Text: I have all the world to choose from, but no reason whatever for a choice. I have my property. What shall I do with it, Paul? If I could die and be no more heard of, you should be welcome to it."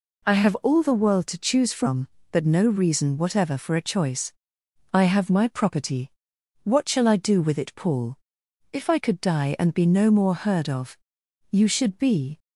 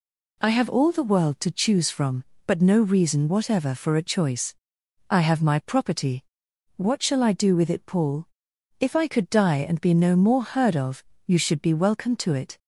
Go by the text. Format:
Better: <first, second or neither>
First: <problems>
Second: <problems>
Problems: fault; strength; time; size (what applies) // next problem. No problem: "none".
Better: second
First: stops before "welcome to it"; at 12.3 s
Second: none